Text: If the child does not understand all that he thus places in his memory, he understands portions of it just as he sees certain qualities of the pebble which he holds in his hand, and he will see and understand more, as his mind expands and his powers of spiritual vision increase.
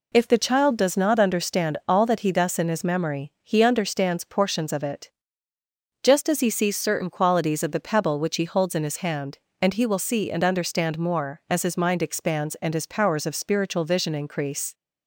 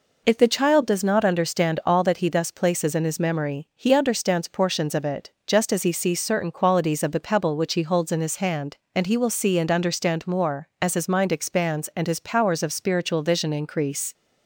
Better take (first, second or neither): second